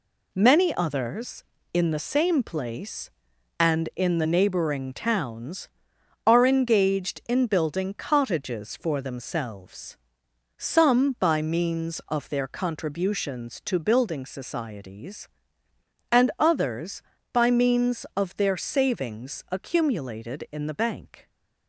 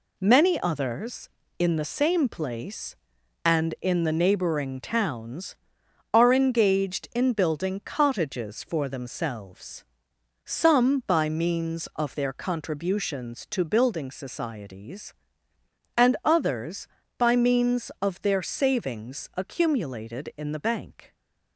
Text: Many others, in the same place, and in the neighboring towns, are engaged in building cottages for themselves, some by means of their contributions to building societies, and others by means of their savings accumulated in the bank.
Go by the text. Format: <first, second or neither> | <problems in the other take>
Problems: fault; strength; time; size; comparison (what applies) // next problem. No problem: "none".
neither | none